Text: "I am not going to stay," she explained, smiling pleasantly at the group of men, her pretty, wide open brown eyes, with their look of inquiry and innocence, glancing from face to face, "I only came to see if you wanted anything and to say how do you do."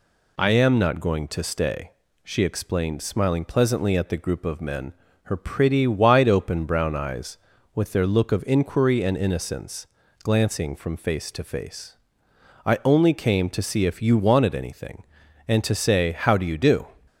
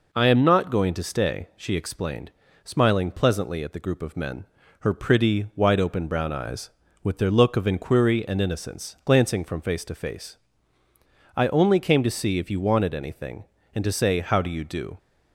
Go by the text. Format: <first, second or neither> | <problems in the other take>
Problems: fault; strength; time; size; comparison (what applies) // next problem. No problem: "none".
neither | none